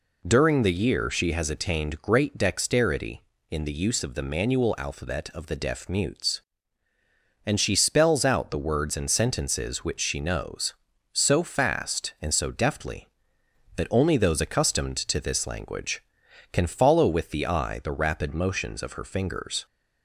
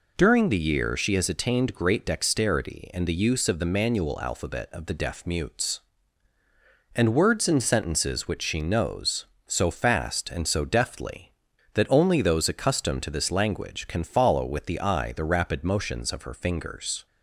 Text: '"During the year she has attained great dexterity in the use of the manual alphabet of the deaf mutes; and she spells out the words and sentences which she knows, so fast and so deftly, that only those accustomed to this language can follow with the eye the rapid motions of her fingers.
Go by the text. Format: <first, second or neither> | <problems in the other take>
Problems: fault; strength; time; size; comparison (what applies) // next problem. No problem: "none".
first | skips "she spells out the"; at 7.1 s